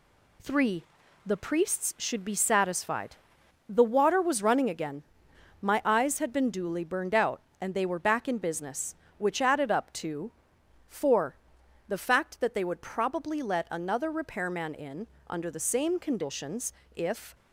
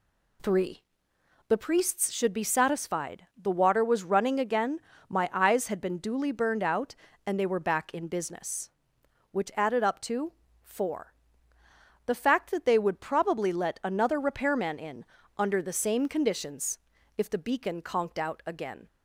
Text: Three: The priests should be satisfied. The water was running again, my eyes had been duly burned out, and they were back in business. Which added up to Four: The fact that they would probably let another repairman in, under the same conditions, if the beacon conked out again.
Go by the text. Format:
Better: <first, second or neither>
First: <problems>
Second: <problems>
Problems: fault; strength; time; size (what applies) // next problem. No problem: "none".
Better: second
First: pauses between "to" and "Four"; noticeable; at 10.3 s; 0.58 s long // stops before "the beacon conked out again"; at 17.3 s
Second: pauses between "to" and "Four"; slight; at 10.3 s; 0.30 s long